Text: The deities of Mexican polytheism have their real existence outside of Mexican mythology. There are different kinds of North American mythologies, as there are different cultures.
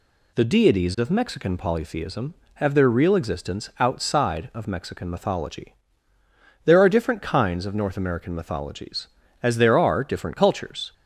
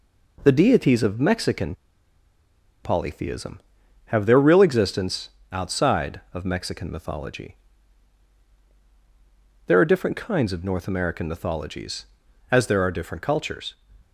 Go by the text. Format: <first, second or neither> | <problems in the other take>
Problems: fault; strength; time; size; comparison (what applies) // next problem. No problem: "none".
first | pauses between "Mexican" and "polytheism"; at 1.7 s; 1.1 s long // pauses between "existence" and "outside"; slight; at 5.2 s; 0.22 s long